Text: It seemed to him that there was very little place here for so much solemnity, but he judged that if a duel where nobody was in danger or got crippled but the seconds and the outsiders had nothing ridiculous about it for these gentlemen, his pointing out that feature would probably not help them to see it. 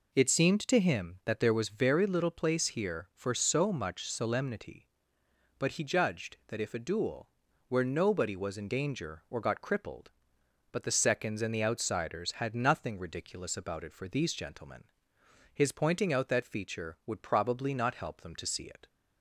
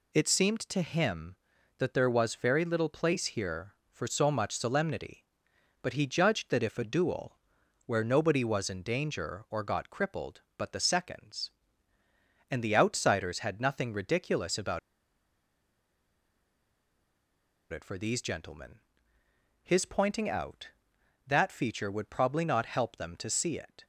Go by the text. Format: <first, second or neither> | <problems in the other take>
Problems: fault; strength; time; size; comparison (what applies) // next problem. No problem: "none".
first | pauses between "duel" and "where"; noticeable; at 7.3 s; 0.50 s long; also in the first // pauses between "about" and "it"; strong; at 14.7 s; 2.9 s long